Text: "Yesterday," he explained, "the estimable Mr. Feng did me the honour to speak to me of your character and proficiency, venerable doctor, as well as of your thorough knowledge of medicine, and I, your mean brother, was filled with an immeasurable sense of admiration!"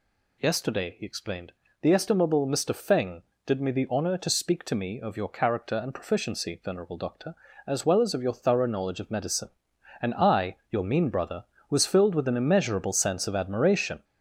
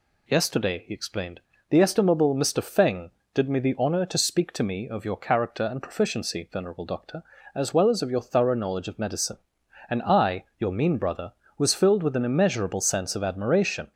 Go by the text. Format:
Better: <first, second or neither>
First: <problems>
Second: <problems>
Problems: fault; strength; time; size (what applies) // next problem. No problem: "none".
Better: second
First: gets louder; noticeable; throughout; 4.5 dB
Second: none